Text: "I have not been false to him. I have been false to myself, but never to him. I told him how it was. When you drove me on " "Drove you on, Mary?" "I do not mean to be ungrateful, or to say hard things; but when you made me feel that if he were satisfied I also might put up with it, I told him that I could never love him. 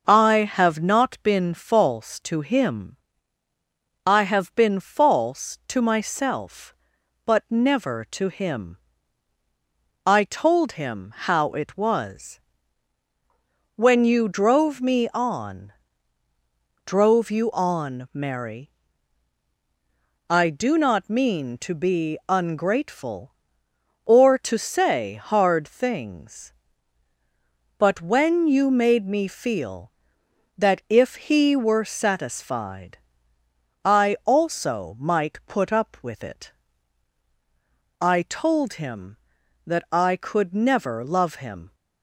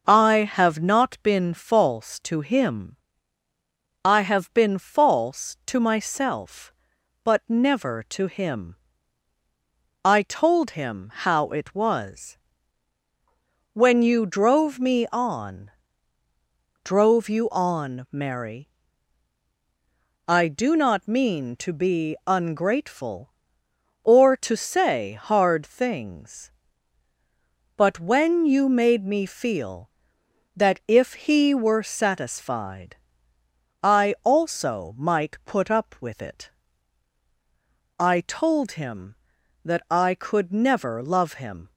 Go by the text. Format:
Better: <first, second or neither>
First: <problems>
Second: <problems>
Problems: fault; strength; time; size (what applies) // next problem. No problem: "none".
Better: neither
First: starts louder than the rest; until 1.0 s; 6.5 dB // pauses between "satisfied" and "I"; noticeable; at 32.9 s; 0.86 s long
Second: starts louder than the rest; until 1.0 s; 6.5 dB // pauses between "satisfied" and "I"; noticeable; at 32.9 s; 0.86 s long